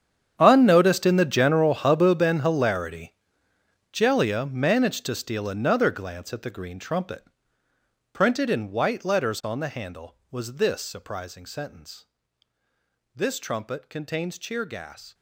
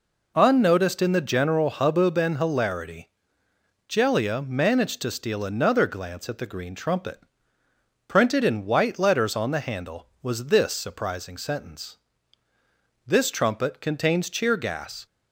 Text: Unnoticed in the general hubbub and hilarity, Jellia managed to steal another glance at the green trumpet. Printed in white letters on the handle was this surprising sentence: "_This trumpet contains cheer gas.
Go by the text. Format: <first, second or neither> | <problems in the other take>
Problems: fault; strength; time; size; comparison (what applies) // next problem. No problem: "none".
second | gets quieter; strong; throughout; 17.5 dB